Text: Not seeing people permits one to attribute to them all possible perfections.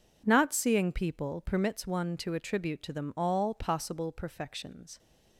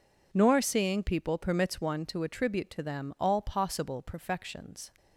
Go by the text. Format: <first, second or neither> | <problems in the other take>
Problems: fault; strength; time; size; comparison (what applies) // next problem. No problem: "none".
first | says "Nor" for "Not"; at 0.3 s